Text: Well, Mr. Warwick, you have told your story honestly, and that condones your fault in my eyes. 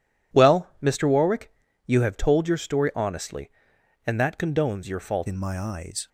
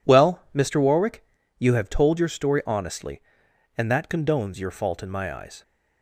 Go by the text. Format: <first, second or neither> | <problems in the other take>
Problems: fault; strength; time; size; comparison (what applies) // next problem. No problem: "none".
second | changes voice at "in"; from 5.2 s on; 0.8 s long